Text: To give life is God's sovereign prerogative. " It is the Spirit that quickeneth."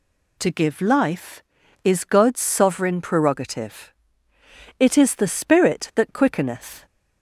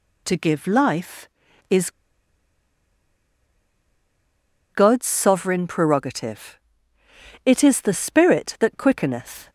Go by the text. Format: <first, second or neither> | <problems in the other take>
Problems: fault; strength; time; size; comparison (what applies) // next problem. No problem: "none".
first | pauses between "is" and "God's"; strong; at 1.8 s; 2.8 s long